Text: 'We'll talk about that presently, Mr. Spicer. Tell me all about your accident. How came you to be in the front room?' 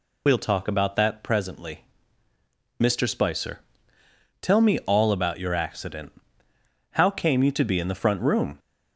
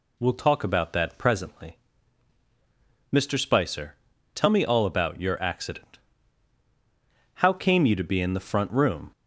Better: second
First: loses the start of "We'll"; at 0.2 s; 55 ms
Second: none

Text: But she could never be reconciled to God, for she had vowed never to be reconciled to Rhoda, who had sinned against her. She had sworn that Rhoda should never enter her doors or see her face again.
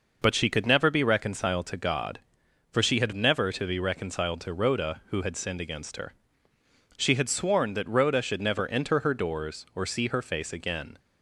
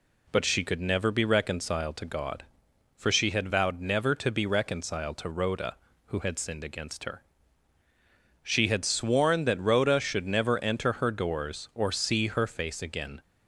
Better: second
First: skips "vowed"; at 3.1 s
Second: none

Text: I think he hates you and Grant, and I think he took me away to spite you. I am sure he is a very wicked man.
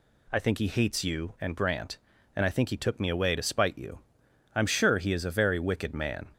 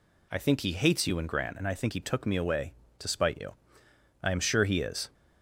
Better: first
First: none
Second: stops before "a very wicked man"; at 5.1 s

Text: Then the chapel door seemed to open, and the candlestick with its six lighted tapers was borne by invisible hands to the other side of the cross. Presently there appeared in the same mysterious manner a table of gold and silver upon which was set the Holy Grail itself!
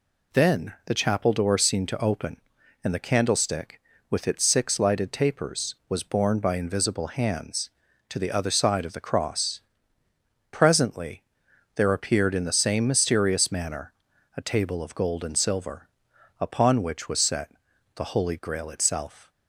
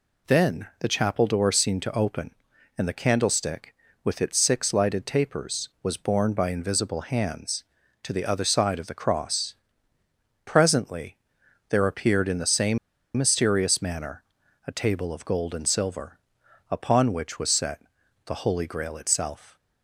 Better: first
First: pauses between "Presently" and "there"; noticeable; at 11.2 s; 0.52 s long // pauses between "manner" and "a"; at 13.9 s; 0.44 s long // pauses between "silver" and "upon"; noticeable; at 15.8 s; 0.52 s long // pauses between "set" and "the"; at 17.5 s; 0.44 s long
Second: pauses between "Presently" and "there"; noticeable; at 11.1 s; 0.52 s long // pauses between "same" and "mysterious"; at 12.7 s; 0.39 s long // pauses between "manner" and "a"; at 14.2 s; 0.44 s long // pauses between "silver" and "upon"; noticeable; at 16.1 s; 0.52 s long // pauses between "set" and "the"; at 17.8 s; 0.44 s long

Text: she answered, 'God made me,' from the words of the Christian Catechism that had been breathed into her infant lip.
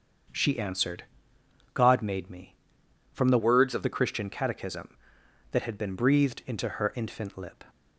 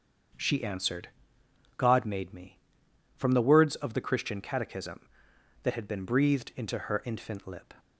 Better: second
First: starts louder than the rest; until 2.0 s; 7 dB // changes voice from "words" to "of"; from 3.3 to 3.8 s; 0.5 s long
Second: starts louder than the rest; strong; until 2.0 s; 7 dB

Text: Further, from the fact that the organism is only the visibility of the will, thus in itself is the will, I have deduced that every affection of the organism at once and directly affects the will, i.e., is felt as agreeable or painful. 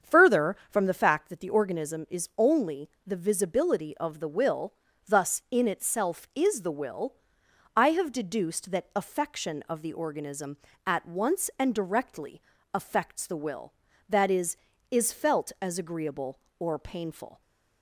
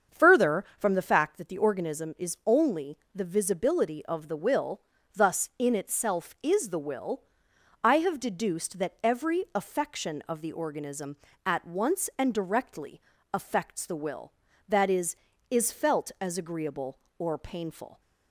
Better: second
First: starts louder than the rest; strong; until 1.1 s; 7.5 dB // pauses between "only" and "the"; slight; at 2.8 s; 0.16 s long // skips "every"; at 8.9 s // pauses between "directly" and "affects"; slight; at 12.4 s; 0.32 s long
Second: starts louder than the rest; strong; until 1.2 s; 7 dB // pauses between "only" and "the"; slight; at 2.9 s; 0.16 s long // pauses between "directly" and "affects"; slight; at 13.0 s; 0.32 s long

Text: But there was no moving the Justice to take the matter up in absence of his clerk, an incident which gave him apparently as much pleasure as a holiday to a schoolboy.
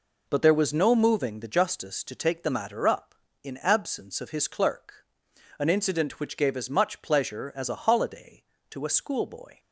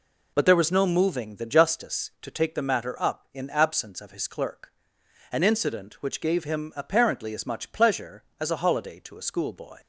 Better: second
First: skips "him apparently"; at 6.5 s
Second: none

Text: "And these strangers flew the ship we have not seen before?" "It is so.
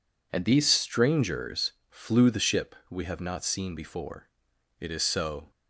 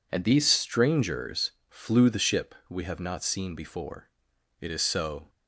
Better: neither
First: pauses between "strangers" and "flew"; slight; at 1.7 s; 0.18 s long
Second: pauses between "strangers" and "flew"; slight; at 1.5 s; 0.18 s long

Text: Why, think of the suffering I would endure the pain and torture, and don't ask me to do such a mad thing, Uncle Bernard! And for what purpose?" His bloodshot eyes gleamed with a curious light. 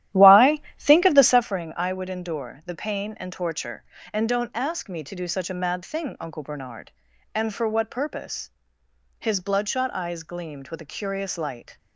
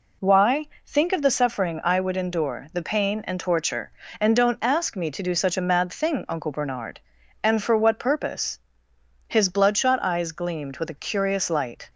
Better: second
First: starts louder than the rest; strong; until 1.6 s; 12.5 dB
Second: none

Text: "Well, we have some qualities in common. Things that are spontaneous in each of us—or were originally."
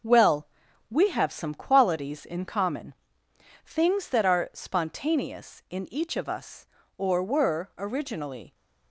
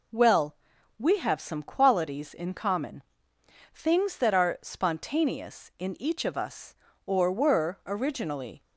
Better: second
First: gets quieter; throughout; 6.5 dB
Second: none

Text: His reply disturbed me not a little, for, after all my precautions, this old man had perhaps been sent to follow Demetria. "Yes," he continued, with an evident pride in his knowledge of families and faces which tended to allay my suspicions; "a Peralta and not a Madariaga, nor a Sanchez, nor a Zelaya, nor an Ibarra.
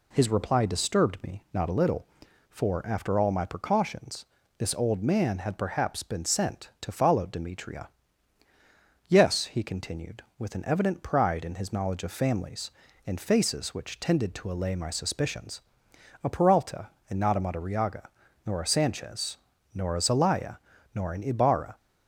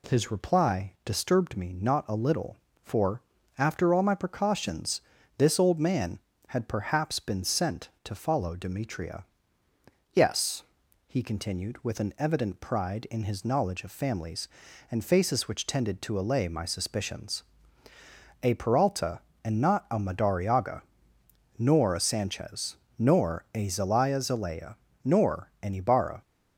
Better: first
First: none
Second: says "Zelaya" twice; at 24.2 s

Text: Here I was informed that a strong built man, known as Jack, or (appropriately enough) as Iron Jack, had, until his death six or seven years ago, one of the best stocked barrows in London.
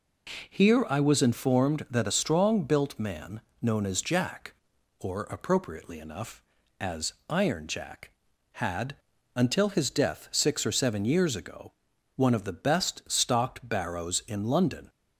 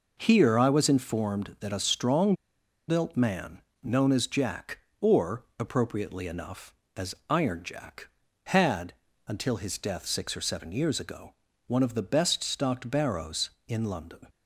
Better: first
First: pauses between "as" and "Iron"; slight; at 7.1 s; 0.16 s long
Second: pauses between "strong" and "built"; noticeable; at 2.3 s; 0.53 s long // pauses between "as" and "Iron"; slight; at 7.1 s; 0.16 s long

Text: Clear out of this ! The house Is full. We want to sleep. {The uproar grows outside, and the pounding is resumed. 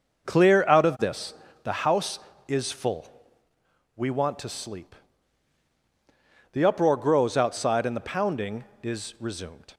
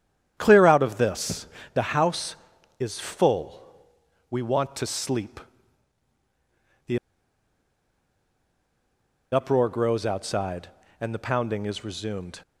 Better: first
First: none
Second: starts louder than the rest; strong; until 1.3 s; 9.5 dB // pauses between "The" and "uproar"; strong; at 6.9 s; 2.3 s long

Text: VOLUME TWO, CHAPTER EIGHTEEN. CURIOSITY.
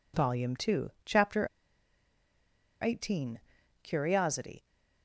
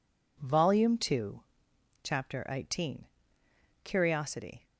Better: second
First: pauses between "CHAPTER" and "EIGHTEEN"; strong; at 1.4 s; 1.3 s long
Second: none

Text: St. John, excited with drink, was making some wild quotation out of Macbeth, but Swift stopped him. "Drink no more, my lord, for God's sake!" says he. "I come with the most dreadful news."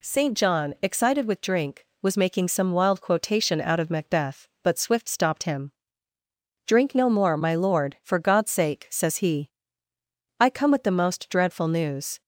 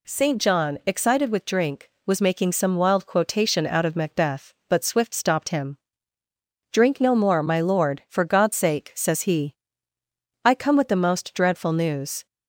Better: neither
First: none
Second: none

